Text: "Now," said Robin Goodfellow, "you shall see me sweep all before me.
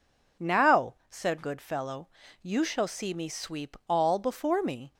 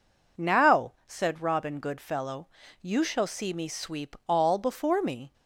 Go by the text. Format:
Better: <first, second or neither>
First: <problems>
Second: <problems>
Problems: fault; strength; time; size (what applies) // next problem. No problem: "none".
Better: second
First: skips "Robin"; at 1.4 s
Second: none